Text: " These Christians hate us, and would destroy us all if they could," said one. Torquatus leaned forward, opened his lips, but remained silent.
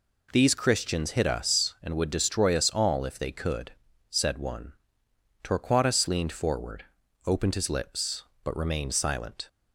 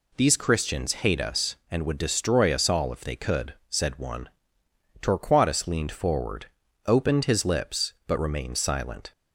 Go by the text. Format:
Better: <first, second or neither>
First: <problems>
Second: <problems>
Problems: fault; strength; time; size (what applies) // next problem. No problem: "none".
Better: second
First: says "hit" for "hate"; at 1.1 s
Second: none